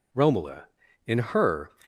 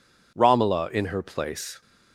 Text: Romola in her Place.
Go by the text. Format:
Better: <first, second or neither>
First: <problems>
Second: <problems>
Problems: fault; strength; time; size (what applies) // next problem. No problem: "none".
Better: second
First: stops before "Place"; at 1.8 s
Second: none